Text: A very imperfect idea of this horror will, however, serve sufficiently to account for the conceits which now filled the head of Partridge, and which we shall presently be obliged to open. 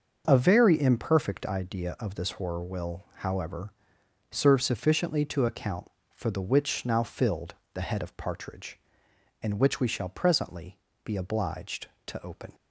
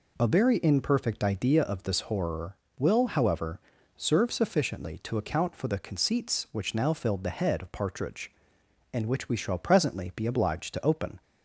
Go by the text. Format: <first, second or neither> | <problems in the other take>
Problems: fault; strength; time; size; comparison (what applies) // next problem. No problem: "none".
second | starts louder than the rest; until 1.2 s; 6.5 dB // skips "conceits"; at 6.4 s // pauses between "filled" and "the"; slight; at 7.5 s; 0.22 s long // pauses between "presently" and "be"; slight; at 10.7 s; 0.26 s long